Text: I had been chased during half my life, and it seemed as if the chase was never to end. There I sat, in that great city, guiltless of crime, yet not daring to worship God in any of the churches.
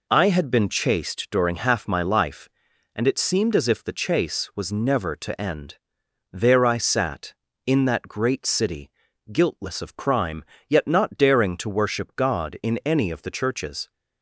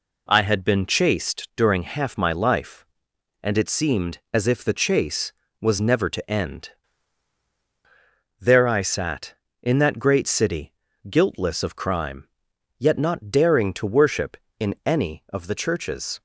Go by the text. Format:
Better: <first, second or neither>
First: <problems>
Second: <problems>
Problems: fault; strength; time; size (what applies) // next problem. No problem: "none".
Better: first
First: none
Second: skips "God"; at 14.4 s